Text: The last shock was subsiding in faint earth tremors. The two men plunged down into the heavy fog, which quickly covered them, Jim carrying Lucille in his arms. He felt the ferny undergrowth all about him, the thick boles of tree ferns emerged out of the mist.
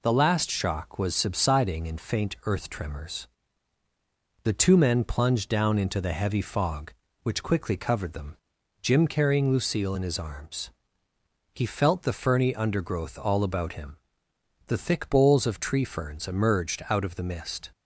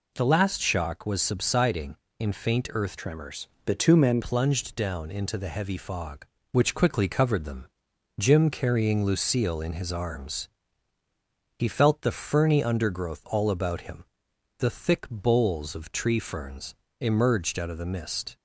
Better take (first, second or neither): first